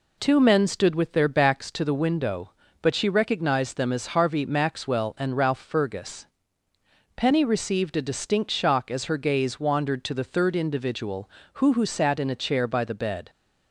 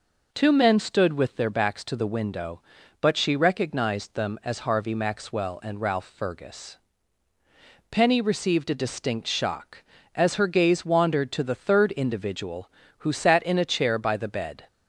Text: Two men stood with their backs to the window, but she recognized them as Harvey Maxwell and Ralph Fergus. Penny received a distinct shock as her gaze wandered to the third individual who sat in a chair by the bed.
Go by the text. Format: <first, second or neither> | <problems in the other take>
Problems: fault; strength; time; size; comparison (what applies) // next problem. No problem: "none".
second | says "who" twice; at 11.7 s